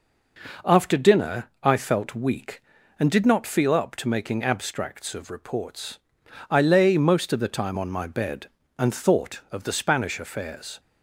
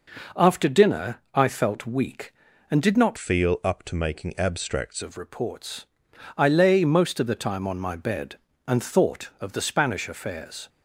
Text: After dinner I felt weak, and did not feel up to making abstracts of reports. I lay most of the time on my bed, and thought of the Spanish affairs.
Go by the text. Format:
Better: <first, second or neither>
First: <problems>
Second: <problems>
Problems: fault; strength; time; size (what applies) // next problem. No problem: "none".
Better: first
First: pauses between "dinner" and "I"; slight; at 1.4 s; 0.16 s long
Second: pauses between "dinner" and "I"; slight; at 1.1 s; 0.16 s long // changes voice from "feel" to "abstracts"; from 3.1 to 5.0 s; 1.9 s long